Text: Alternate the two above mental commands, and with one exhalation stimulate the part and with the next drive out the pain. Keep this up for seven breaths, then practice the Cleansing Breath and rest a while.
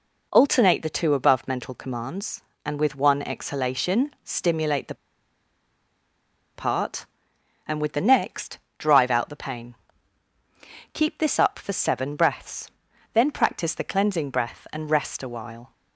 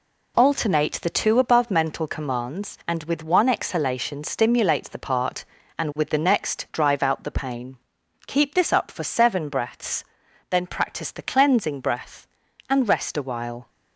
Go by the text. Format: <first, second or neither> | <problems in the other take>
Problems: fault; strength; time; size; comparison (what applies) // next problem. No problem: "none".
second | pauses between "the" and "part"; strong; at 4.9 s; 1.6 s long // pauses between "next" and "drive"; slight; at 8.5 s; 0.18 s long